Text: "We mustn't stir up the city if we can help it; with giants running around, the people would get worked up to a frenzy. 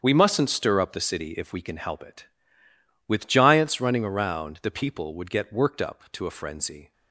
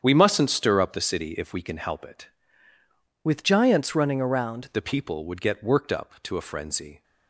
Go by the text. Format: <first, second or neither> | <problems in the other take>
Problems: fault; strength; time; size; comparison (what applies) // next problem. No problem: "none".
first | starts louder than the rest; strong; until 1.0 s; 8 dB; strong in the first // changes voice from "with" to "around"; from 3.2 to 4.6 s; 1.4 s long